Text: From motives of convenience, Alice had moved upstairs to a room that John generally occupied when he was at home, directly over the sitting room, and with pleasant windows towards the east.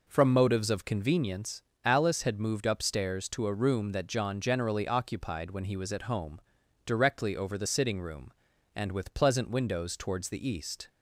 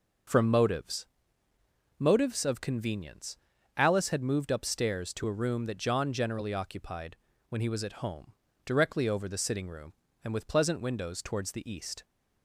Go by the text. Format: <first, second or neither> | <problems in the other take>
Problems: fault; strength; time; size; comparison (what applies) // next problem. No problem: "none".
first | starts louder than the rest; until 2.2 s; 6.5 dB // says "motives" twice; at 1.9 s // pauses between "occupied" and "when"; slight; at 7.1 s; 0.32 s long